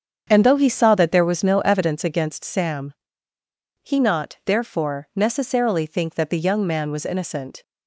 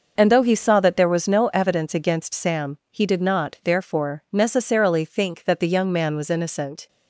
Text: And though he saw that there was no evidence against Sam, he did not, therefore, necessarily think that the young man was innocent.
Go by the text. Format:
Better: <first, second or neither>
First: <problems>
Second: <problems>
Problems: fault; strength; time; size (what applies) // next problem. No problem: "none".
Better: second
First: starts louder than the rest; strong; until 1.3 s; 7.5 dB // skips "did"; at 3.9 s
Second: none